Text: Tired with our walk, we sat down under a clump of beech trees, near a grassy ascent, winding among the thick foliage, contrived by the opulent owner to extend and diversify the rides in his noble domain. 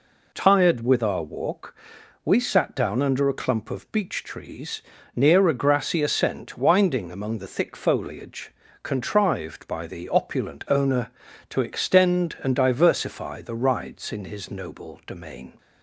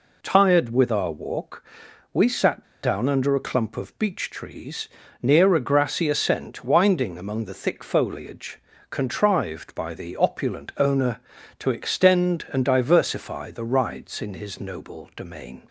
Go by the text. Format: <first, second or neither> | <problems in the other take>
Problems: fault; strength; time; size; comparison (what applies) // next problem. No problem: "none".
first | pauses between "sat" and "down"; slight; at 2.6 s; 0.18 s long